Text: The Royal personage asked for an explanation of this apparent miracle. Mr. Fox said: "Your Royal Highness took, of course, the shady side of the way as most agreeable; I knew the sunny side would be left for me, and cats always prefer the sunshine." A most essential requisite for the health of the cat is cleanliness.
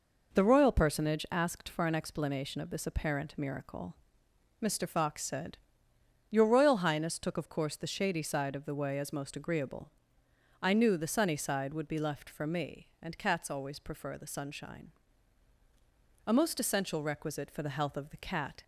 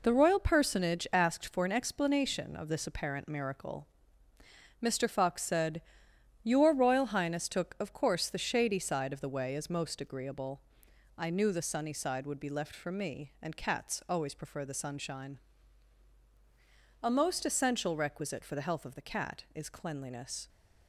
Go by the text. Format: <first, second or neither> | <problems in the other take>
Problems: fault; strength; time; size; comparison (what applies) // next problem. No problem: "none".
second | stops before "is cleanliness"; at 18.6 s